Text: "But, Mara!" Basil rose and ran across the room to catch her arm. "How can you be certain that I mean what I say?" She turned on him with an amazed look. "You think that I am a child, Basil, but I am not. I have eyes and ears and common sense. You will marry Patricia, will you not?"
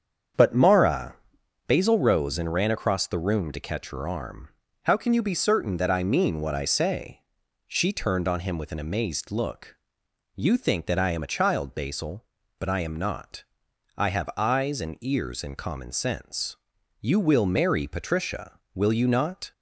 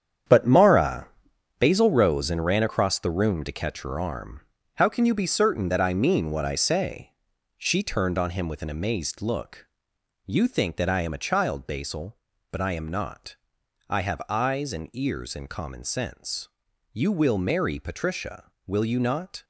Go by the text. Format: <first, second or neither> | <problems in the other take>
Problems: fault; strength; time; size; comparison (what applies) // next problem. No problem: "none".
first | gets quieter; strong; throughout; 10 dB // starts louder than the rest; strong; until 1.8 s; 8.5 dB; strong in the first